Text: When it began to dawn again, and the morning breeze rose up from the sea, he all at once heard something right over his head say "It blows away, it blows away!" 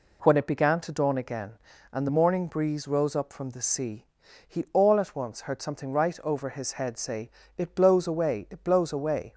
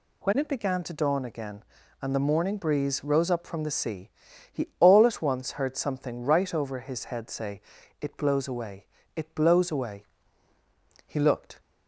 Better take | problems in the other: first | pauses between "say" and "It"; at 7.5 s; 0.40 s long; slight in the first // goes on to say "He looked"; from 11.0 s on; 0.54 s long

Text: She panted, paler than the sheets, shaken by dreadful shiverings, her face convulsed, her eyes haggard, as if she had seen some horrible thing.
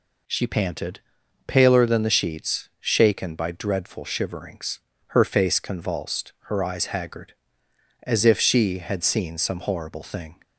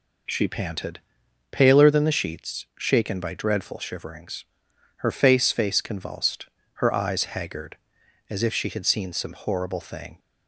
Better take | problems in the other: first | says "face" twice; at 5.5 s

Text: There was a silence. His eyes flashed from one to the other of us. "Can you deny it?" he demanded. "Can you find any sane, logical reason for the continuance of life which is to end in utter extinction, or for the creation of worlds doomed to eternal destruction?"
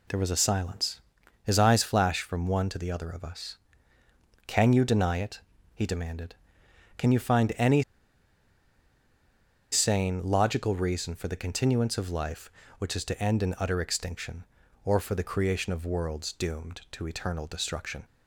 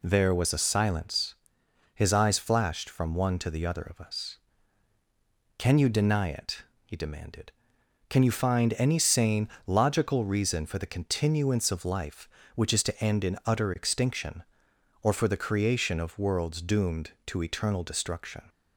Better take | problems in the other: second | pauses between "any" and "sane"; strong; at 7.8 s; 1.9 s long

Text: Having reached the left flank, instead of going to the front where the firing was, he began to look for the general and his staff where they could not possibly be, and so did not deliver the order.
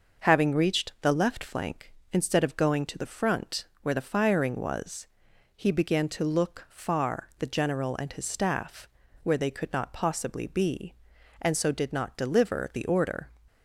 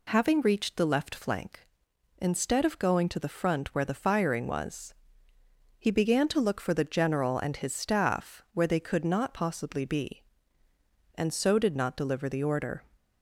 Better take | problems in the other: second | starts louder than the rest; noticeable; until 1.3 s; 6 dB // pauses between "front" and "where"; slight; at 3.6 s; 0.18 s long // says "far" for "for"; at 6.6 s // pauses between "staff" and "where"; slight; at 8.8 s; 0.36 s long

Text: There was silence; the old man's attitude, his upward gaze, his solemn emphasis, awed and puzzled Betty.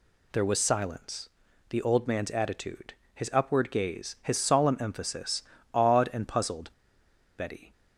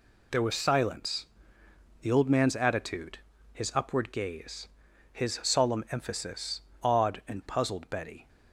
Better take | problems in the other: second | pauses between "puzzled" and "Betty"; noticeable; at 6.6 s; 0.68 s long

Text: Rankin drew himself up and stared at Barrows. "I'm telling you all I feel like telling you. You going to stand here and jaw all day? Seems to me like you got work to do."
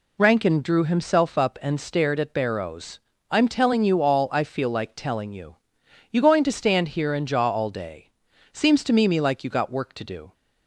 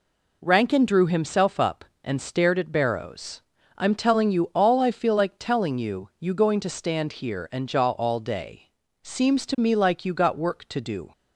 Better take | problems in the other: second | says "me" twice; at 9.0 s

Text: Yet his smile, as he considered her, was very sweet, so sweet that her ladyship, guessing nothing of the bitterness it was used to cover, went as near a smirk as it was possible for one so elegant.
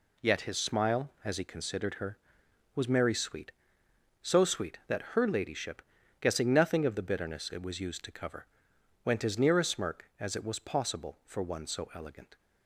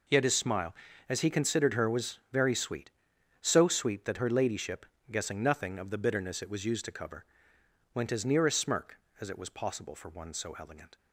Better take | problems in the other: second | says "merry" for "very"; at 2.8 s

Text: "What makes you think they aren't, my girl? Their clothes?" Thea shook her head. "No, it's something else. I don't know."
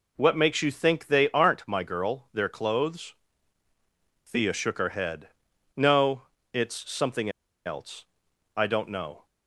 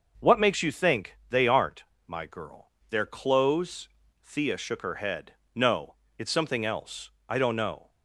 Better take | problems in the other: second | pauses between "something" and "else"; at 7.2 s; 0.36 s long

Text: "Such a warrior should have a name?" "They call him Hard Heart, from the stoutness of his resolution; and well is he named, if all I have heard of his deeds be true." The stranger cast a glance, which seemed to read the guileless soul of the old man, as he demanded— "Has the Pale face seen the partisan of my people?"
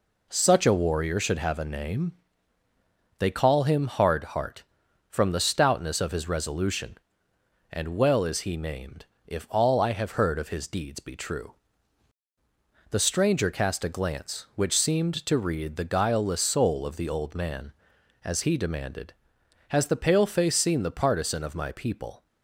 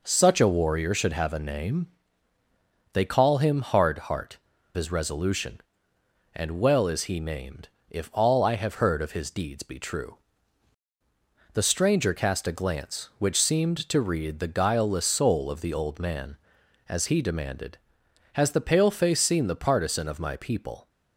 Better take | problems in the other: first | skips "from the stoutness of"; at 4.5 s

